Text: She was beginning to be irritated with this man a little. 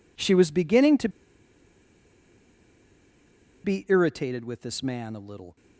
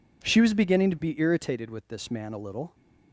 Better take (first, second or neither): second